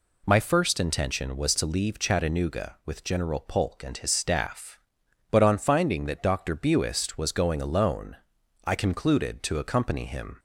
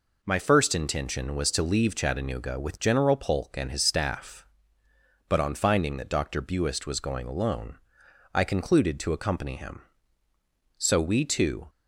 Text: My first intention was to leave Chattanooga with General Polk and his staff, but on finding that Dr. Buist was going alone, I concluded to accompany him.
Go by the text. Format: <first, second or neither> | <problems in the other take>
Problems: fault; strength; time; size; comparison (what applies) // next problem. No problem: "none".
first | goes on to say "So we two"; noticeable; from 10.7 s on; 0.90 s long